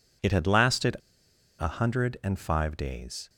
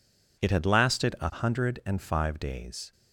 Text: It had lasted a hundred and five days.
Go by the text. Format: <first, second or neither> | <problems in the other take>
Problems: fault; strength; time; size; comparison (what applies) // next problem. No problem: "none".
second | pauses between "lasted" and "a"; noticeable; at 0.9 s; 0.62 s long